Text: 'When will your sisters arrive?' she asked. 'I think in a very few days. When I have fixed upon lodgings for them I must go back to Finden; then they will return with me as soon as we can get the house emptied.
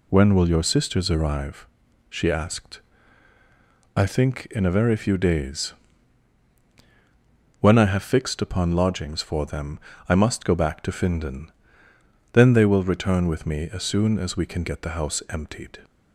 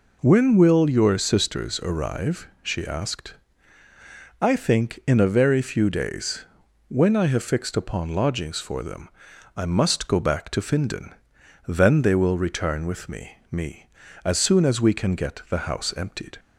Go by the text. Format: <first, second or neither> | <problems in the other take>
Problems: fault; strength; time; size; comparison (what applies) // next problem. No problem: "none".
first | pauses between "them" and "I"; noticeable; at 9.0 s; 0.46 s long; slight in the first // says "me" twice; at 13.5 s